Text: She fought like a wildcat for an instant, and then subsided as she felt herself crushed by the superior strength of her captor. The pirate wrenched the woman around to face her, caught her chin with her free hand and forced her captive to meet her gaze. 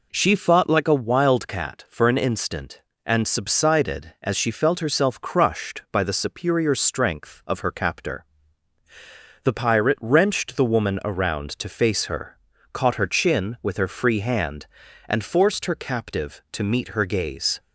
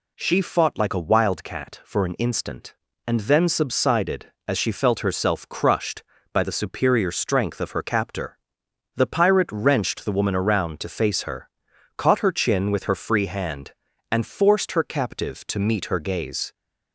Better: second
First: skips "then"; at 3.2 s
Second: none

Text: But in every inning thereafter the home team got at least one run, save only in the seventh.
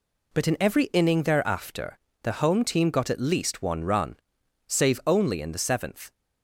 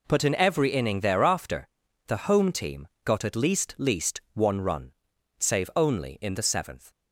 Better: first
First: pauses between "thereafter" and "the"; slight; at 1.9 s; 0.26 s long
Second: pauses between "thereafter" and "the"; at 1.6 s; 0.40 s long // pauses between "team" and "got"; slight; at 2.8 s; 0.16 s long // says "least" twice; at 3.7 s

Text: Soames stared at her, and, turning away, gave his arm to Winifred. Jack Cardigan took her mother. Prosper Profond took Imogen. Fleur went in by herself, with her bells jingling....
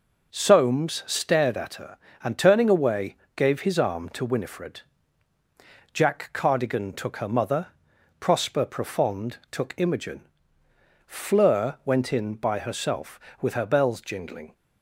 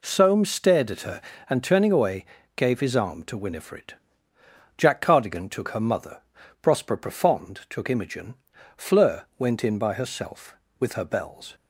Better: first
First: none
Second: stops before "jingling"; at 11.5 s

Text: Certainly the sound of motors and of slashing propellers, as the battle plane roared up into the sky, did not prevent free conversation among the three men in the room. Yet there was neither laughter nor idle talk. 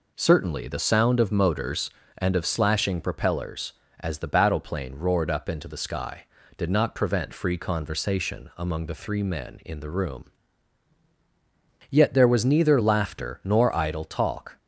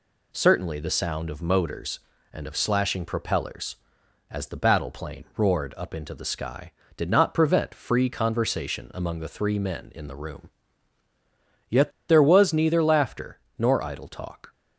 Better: first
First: none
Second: pauses between "Yet" and "there"; slight; at 11.9 s; 0.17 s long // pauses between "laughter" and "nor"; slight; at 13.3 s; 0.20 s long

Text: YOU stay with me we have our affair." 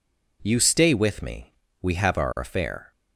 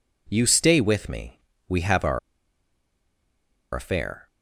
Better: first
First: pauses between "me" and "we"; slight; at 1.5 s; 0.30 s long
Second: pauses between "me" and "we"; slight; at 1.3 s; 0.30 s long // pauses between "our" and "affair"; strong; at 2.1 s; 1.5 s long

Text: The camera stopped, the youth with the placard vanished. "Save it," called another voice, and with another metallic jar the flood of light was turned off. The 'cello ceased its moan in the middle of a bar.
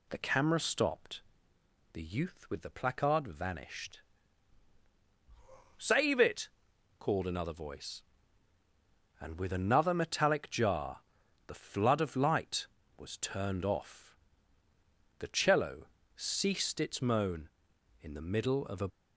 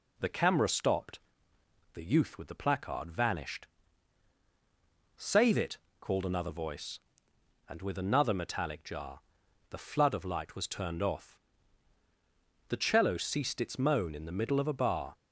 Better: second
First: pauses between "jar" and "the"; noticeable; at 11.0 s; 0.46 s long // pauses between "cello" and "ceased"; slight; at 15.8 s; 0.28 s long // stops before "bar"; at 18.8 s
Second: pauses between "jar" and "the"; noticeable; at 9.2 s; 0.48 s long

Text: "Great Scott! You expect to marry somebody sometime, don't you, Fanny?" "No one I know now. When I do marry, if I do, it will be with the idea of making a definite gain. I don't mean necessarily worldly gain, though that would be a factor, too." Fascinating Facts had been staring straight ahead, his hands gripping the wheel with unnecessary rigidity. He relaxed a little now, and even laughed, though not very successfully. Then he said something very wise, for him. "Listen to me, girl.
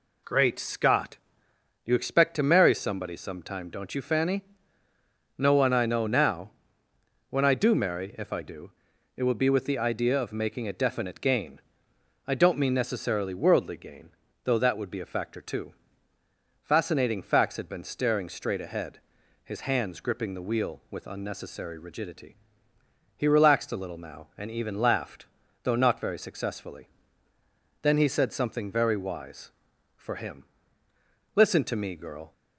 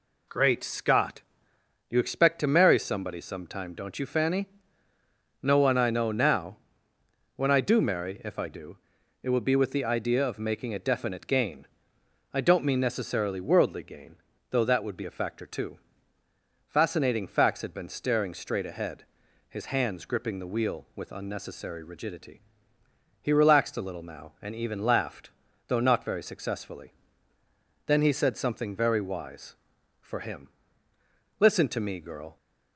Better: neither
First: none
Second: none

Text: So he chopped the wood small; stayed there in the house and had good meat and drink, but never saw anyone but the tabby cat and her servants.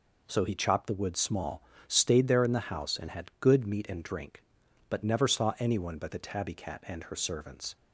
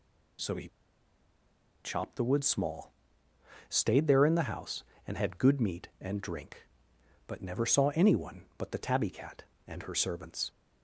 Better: first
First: none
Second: pauses between "he" and "chopped"; at 0.6 s; 1.1 s long

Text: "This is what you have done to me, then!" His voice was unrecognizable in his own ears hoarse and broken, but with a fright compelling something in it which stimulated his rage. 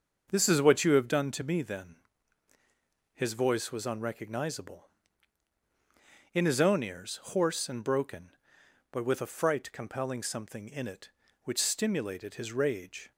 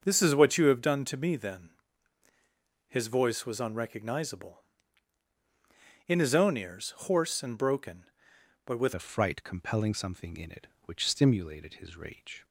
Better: first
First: starts louder than the rest; until 1.3 s; 6.5 dB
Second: starts louder than the rest; until 1.0 s; 6.5 dB // changes voice at "a"; from 8.9 s on; 3.5 s long

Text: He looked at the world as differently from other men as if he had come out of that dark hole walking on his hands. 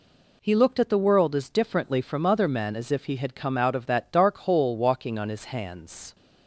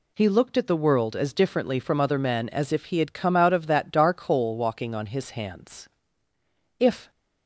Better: first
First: none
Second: goes on to say "If"; slight; from 6.7 s on; 0.32 s long

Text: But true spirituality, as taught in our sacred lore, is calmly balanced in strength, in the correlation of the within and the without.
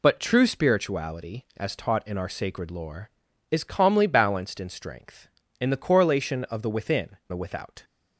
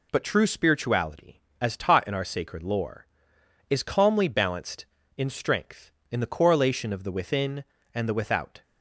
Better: second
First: skips "and"; at 7.2 s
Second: none

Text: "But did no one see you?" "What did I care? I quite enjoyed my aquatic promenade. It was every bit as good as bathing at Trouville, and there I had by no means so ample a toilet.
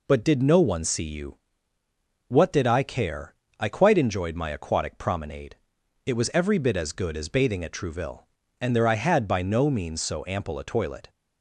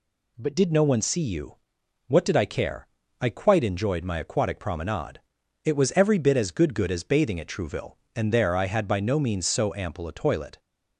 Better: first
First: none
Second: says "good" twice; at 6.7 s

